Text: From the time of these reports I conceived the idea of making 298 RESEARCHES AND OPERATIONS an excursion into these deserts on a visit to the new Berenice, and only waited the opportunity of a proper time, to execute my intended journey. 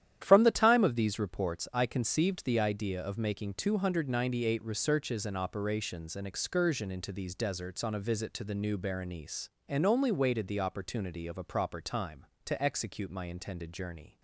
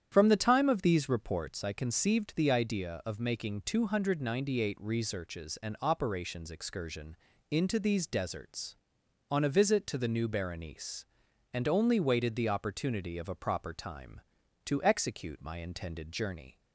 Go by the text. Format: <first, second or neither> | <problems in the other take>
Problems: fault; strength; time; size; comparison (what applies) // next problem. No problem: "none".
first | starts louder than the rest; strong; until 1.1 s; 9 dB; strong in the first // skips "an"; at 6.5 s // pauses between "excursion" and "into"; slight; at 7.1 s; 0.32 s long